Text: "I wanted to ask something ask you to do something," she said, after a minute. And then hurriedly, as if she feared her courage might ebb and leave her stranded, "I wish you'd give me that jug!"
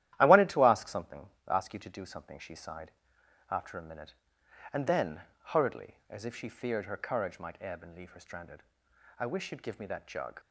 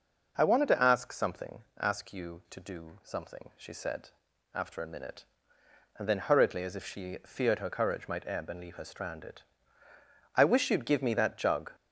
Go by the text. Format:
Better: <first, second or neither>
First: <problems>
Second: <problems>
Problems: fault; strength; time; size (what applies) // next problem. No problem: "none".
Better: second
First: starts louder than the rest; strong; until 1.2 s; 13 dB // pauses between "something" and "ask"; slight; at 1.2 s; 0.20 s long // says "sighed" for "said"; at 2.5 s // pauses between "then" and "hurriedly"; slight; at 5.2 s; 0.24 s long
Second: pauses between "something" and "ask"; slight; at 1.6 s; 0.18 s long